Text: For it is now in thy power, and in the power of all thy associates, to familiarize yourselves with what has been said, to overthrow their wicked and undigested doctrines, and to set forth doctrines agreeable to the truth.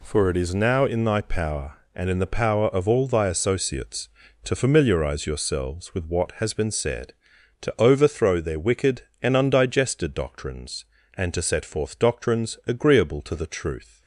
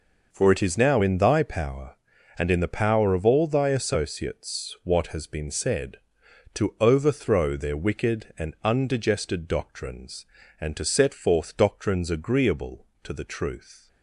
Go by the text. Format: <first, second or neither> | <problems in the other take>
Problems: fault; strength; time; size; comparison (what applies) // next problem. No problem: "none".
first | skips "to familiarize yourselves with"; at 4.8 s